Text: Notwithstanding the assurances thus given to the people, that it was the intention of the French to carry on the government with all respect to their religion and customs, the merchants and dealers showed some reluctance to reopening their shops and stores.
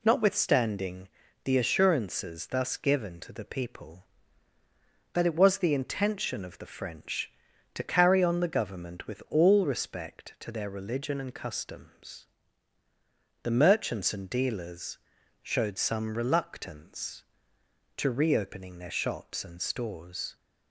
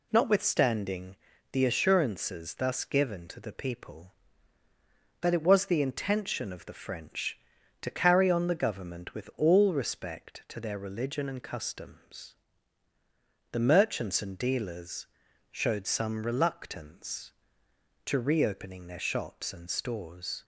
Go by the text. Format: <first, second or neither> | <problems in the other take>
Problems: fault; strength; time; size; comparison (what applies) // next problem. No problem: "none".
neither | pauses between "Notwithstanding" and "the"; slight; the same in both // pauses between "dealers" and "showed"; noticeable; the same in both